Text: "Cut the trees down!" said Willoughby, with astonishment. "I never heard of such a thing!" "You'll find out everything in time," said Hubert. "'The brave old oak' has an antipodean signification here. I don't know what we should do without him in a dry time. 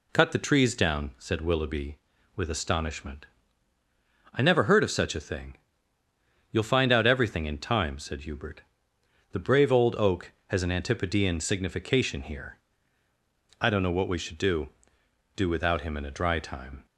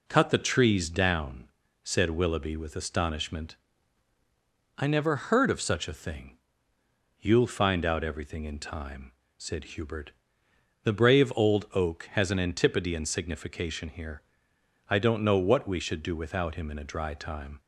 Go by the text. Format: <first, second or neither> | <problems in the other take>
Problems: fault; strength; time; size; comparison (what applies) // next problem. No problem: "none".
second | says "do" twice; at 15.3 s